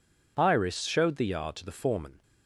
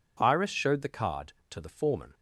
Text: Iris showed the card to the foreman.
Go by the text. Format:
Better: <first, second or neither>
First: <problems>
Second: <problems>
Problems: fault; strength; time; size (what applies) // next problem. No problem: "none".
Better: second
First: says "yard" for "card"; at 1.2 s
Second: none